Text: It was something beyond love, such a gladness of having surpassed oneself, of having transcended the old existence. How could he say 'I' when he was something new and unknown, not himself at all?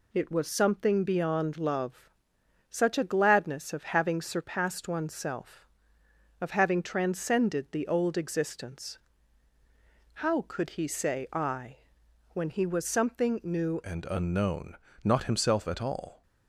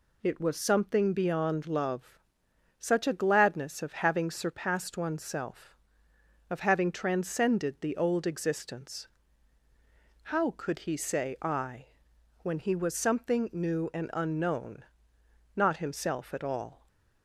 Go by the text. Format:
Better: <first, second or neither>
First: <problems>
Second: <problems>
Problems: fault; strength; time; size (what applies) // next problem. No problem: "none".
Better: second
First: pauses between "I" and "when"; noticeable; at 11.7 s; 0.56 s long // changes voice at "and"; from 13.8 s on; 2.4 s long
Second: pauses between "I" and "when"; noticeable; at 11.8 s; 0.56 s long